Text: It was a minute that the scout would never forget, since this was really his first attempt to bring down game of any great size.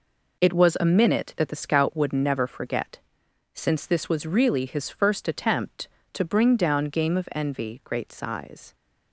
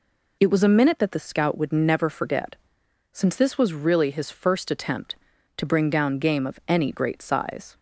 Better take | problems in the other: second | says "envy" for "any"; at 7.3 s

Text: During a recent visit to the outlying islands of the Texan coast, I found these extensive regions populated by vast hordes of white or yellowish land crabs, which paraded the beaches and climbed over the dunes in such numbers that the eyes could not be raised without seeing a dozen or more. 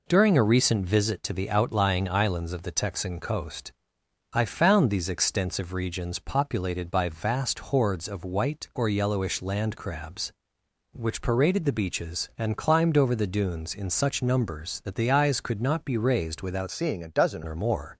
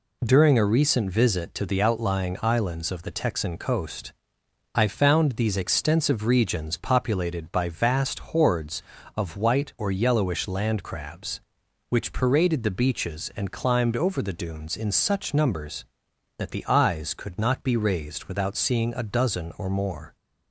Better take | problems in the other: second | changes voice from "seeing" to "dozen"; from 16.7 to 17.4 s; 0.7 s long

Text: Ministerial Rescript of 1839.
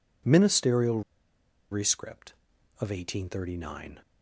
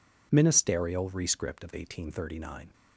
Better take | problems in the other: second | pauses between "Ministerial" and "Rescript"; noticeable; at 1.0 s; 0.70 s long

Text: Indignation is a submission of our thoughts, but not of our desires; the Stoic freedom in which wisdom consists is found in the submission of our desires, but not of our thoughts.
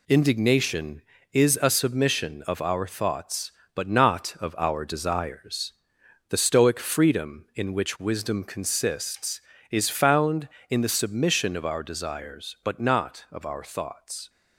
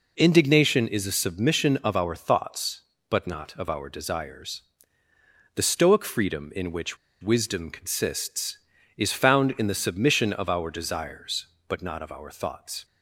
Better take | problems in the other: first | pauses between "which" and "wisdom"; slight; at 6.9 s; 0.23 s long

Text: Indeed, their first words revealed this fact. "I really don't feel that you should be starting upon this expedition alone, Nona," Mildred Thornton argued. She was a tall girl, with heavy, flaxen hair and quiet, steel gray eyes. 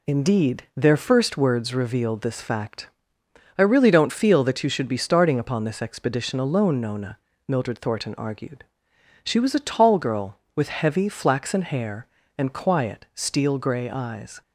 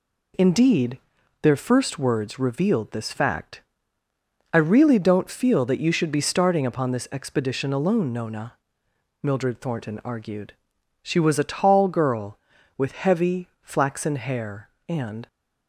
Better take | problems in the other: first | stops before "quiet steel gray eyes"; at 15.2 s

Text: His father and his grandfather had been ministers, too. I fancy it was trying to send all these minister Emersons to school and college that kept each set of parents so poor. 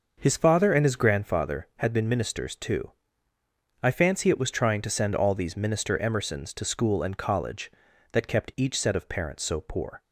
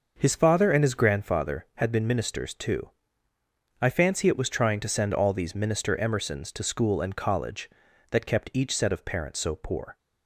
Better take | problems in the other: neither | starts louder than the rest; noticeable; the same in both

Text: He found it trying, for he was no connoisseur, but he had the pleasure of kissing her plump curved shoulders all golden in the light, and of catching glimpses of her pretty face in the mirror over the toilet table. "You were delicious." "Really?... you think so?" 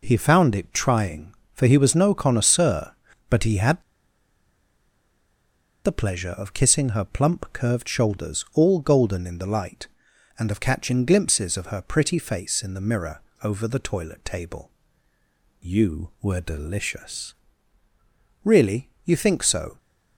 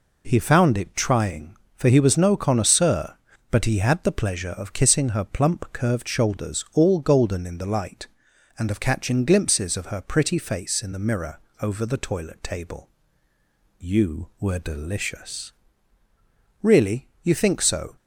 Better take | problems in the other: second | pauses between "had" and "the"; strong; at 3.8 s; 2.0 s long // pauses between "mirror" and "over"; slight; at 13.2 s; 0.22 s long; slight in the second

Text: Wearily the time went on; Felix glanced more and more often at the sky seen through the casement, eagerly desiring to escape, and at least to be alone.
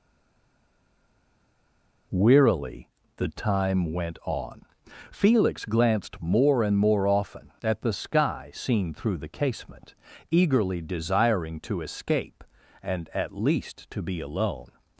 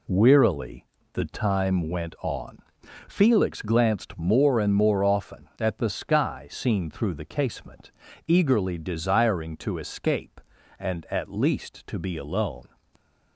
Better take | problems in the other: second | stays silent before the first word; noticeable; until 2.1 s; 2.1 s long // pauses between "Wearily" and "the"; slight; at 2.8 s; 0.30 s long; slight in the second

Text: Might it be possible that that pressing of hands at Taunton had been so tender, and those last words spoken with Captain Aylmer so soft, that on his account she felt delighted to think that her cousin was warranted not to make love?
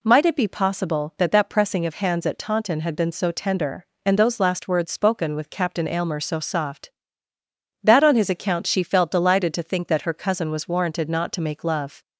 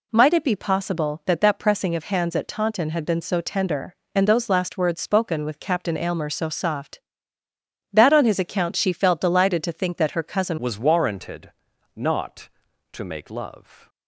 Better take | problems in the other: first | changes voice at "was"; from 10.5 s on; 3.3 s long // pauses between "warranted" and "not"; noticeable; at 11.5 s; 0.46 s long

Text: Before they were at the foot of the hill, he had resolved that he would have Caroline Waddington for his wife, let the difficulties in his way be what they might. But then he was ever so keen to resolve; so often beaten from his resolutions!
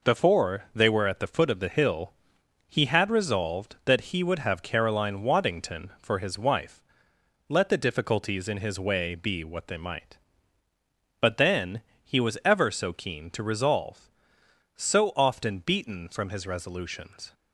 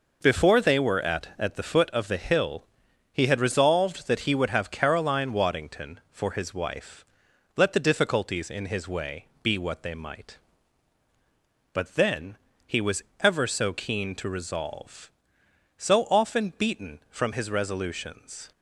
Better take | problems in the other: first | says "at" twice; at 1.3 s // pauses between "way" and "be"; slight; at 9.2 s; 0.16 s long // pauses between "then" and "he"; slight; at 12.3 s; 0.32 s long; slight in the first // pauses between "was" and "ever"; slight; at 13.0 s; 0.18 s long

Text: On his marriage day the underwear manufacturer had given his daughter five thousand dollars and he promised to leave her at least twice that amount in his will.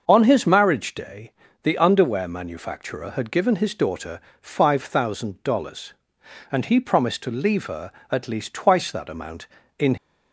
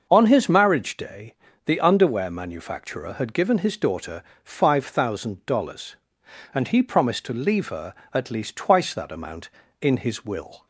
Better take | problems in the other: second | starts louder than the rest; until 1.0 s; 6.5 dB; also in the second // pauses between "day" and "the"; slight; at 1.3 s; 0.32 s long; slight in the second // pauses between "daughter" and "five"; slight; at 4.2 s; 0.18 s long; slight in the second // stops before "his will"; at 9.9 s

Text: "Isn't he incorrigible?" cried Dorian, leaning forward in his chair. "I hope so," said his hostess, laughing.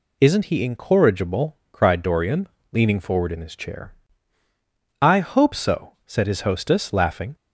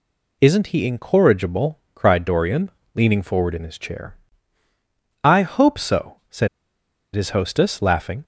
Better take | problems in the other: first | pauses between "said" and "his"; noticeable; at 6.4 s; 0.67 s long

